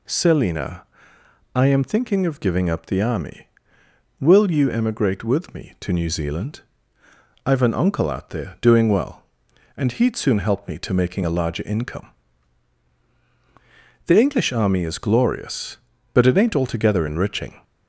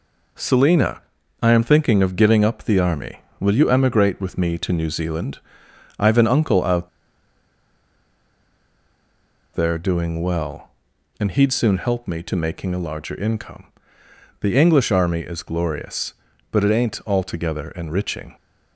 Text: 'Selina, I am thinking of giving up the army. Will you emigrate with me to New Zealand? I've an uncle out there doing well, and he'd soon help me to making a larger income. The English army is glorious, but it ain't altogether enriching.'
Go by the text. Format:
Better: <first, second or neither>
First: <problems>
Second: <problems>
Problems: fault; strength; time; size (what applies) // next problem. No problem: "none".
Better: first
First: none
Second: pauses between "out" and "there"; strong; at 6.8 s; 2.6 s long